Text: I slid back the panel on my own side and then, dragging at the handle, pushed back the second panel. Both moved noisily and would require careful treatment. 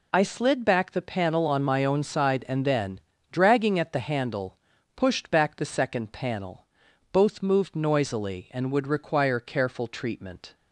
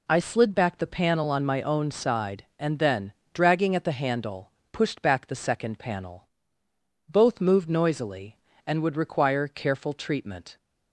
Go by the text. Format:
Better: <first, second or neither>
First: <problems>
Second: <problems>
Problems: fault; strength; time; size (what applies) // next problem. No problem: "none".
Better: neither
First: none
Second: none